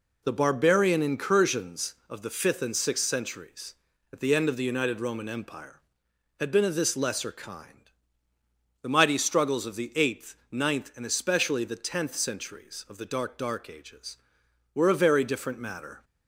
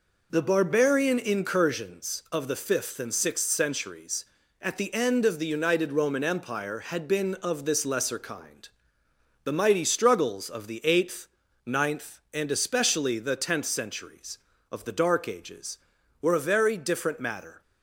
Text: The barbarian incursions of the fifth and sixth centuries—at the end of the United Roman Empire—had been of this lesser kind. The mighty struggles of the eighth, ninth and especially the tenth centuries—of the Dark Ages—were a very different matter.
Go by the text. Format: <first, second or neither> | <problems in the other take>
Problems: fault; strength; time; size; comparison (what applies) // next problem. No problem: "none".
second | says "Dark" twice; at 13.3 s